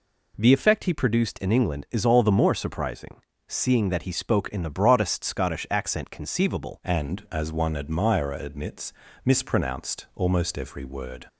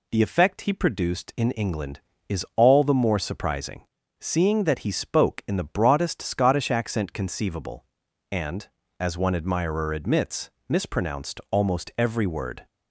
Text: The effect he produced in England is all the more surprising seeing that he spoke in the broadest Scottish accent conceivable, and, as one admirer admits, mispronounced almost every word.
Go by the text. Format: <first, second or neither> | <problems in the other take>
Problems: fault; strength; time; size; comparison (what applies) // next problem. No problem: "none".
second | pauses between "surprising" and "seeing"; slight; at 3.2 s; 0.26 s long; slight in the second // changes voice at "and"; from 6.8 s on; 4.4 s long